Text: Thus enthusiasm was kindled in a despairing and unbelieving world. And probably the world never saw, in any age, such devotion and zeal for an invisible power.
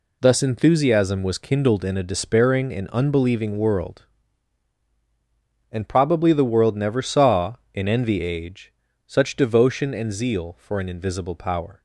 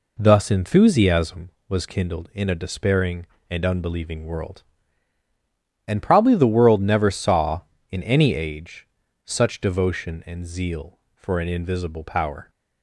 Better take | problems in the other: second | says "envy" for "any"; at 7.8 s

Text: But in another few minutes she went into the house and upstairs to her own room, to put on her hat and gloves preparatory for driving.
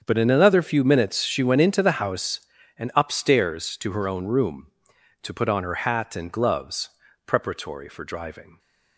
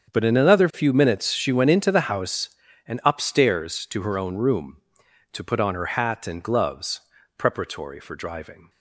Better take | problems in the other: neither | starts louder than the rest; strong; the same in both // pauses between "gloves" and "preparatory"; slight; the same in both

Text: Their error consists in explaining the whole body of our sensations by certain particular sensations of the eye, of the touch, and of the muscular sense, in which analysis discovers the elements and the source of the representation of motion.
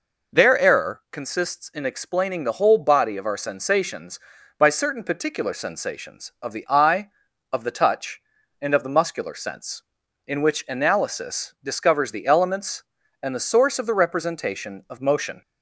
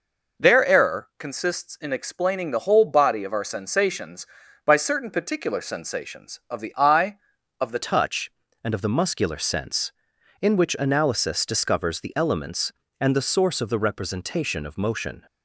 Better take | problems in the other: first | changes voice at "touch"; from 7.8 s on; 7.4 s long

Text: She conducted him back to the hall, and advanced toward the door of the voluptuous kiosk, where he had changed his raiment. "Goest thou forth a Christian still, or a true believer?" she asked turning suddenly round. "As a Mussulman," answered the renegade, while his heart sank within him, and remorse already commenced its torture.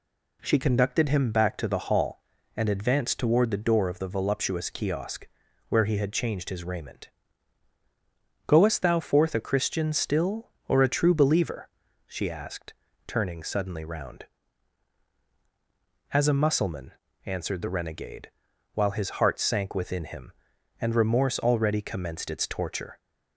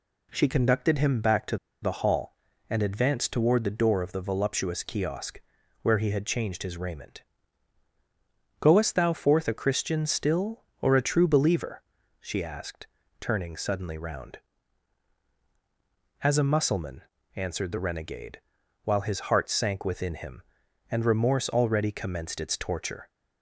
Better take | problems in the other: first | pauses between "to" and "the"; slight; at 1.5 s; 0.24 s long // pauses between "asked" and "turning"; slight; at 12.8 s; 0.34 s long; slight in the first

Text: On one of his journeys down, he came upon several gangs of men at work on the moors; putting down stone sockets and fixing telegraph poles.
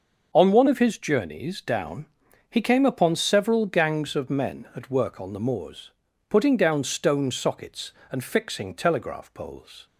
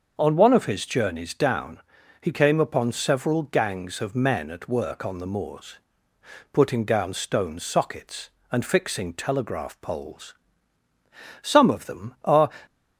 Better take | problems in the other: first | starts louder than the rest; until 1.1 s; 6.5 dB; noticeable in the first // goes on to say "Some of them are"; noticeable; from 11.4 s on; 1.0 s long

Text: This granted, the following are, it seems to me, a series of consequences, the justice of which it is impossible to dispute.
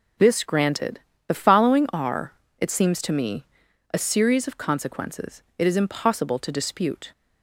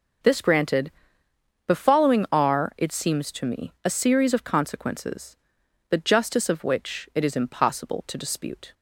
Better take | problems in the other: second | skips "the justice of which"; at 5.5 s

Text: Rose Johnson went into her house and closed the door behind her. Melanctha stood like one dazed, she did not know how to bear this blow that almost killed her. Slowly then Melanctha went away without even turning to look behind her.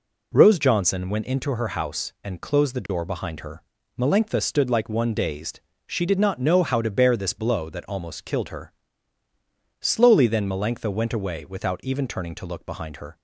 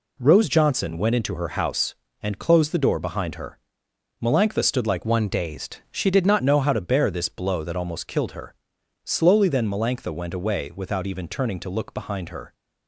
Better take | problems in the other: first | changes voice from "one" to "not"; from 5.0 to 6.4 s; 1.4 s long

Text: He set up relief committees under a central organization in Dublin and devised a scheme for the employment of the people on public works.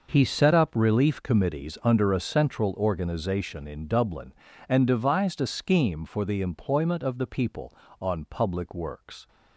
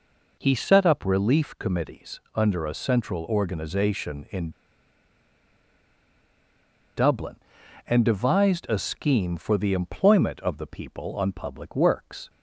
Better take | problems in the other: first | pauses between "committees" and "under"; slight; at 2.1 s; 0.16 s long // pauses between "in" and "Dublin"; strong; at 4.4 s; 2.4 s long

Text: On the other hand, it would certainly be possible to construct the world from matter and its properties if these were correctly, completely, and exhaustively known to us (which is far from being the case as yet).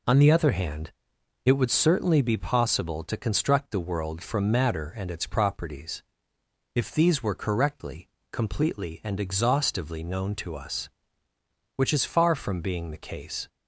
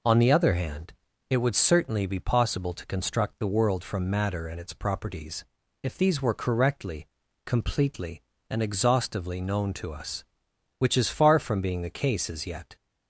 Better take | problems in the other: second | pauses between "properties" and "if"; noticeable; at 6.0 s; 0.72 s long; also in the second // stops before "as yet"; at 13.4 s

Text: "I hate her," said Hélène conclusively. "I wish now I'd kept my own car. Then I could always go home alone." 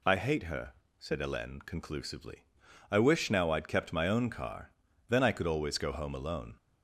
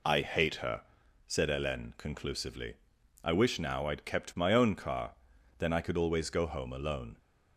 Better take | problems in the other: neither | none

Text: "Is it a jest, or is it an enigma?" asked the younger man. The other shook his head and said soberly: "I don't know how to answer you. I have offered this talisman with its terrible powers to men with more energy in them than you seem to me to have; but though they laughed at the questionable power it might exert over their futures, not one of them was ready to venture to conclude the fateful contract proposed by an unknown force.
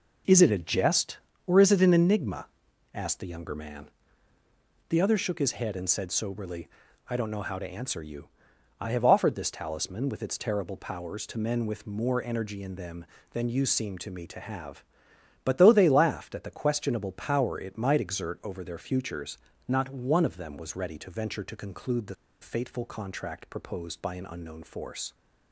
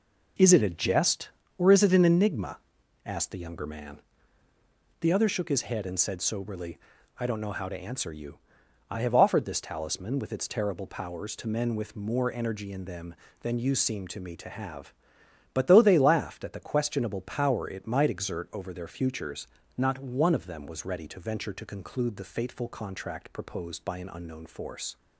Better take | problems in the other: second | pauses between "the" and "fateful"; slight; at 22.1 s; 0.29 s long

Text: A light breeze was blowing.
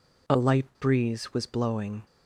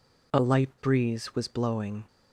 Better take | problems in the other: neither | none

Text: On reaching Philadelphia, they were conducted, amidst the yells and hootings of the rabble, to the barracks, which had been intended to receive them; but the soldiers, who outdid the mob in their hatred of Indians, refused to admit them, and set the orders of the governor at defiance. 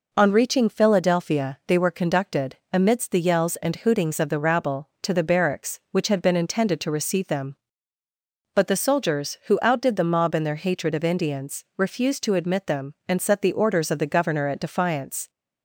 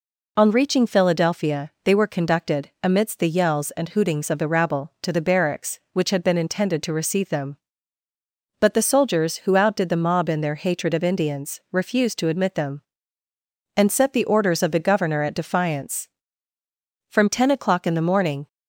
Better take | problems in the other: first | goes on to say "From ten o'clock in the morning"; from 17.0 s on; 1.3 s long

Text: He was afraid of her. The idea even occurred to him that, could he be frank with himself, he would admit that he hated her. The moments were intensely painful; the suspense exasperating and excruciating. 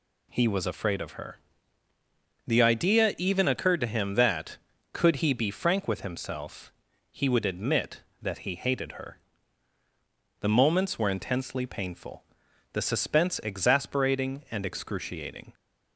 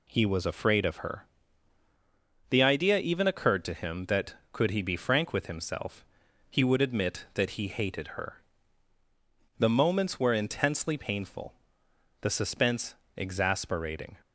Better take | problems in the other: first | pauses between "suspense" and "exasperating"; slight; at 12.9 s; 0.22 s long // stops before "and excruciating"; at 14.2 s

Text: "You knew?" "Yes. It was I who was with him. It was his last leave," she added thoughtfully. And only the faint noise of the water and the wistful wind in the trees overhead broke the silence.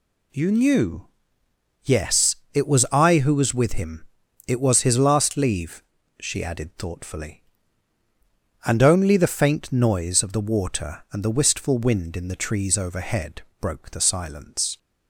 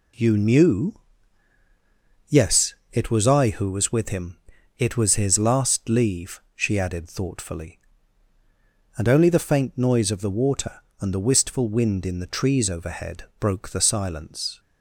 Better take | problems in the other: neither | pauses between "overhead" and "broke"; slight; the same in both

